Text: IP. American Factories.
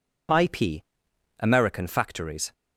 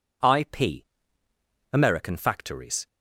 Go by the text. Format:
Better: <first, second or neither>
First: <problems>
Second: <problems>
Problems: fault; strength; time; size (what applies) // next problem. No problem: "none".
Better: neither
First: none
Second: none